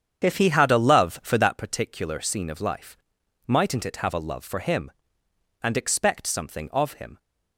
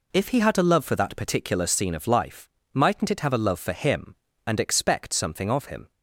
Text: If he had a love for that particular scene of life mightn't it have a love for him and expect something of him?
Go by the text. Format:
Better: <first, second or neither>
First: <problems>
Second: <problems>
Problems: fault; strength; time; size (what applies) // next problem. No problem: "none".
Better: second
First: starts louder than the rest; strong; until 1.5 s; 8 dB // pauses between "life" and "mightn't"; noticeable; at 2.9 s; 0.50 s long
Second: pauses between "life" and "mightn't"; slight; at 2.4 s; 0.24 s long